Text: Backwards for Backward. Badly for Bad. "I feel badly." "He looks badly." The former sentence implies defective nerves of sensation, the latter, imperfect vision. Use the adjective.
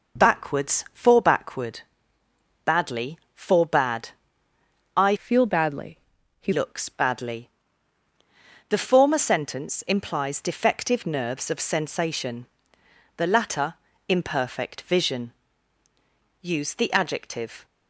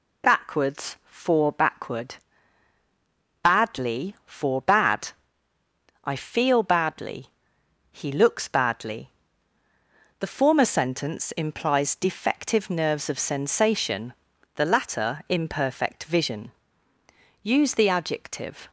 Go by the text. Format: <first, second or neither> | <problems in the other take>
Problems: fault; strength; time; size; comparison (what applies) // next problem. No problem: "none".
second | changes voice from "feel" to "He"; from 5.1 to 6.5 s; 1.4 s long